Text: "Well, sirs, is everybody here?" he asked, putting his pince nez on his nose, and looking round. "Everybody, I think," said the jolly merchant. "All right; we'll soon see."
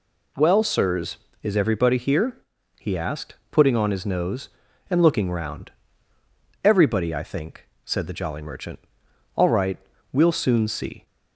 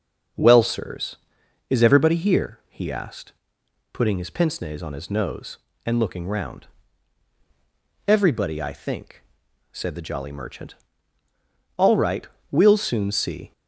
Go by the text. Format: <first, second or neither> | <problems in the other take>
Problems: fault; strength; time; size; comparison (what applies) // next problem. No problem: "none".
second | skips "his pince nez"; at 3.7 s